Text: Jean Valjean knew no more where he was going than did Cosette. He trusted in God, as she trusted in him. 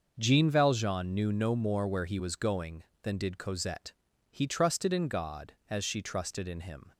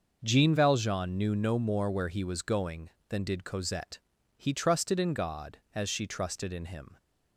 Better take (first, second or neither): neither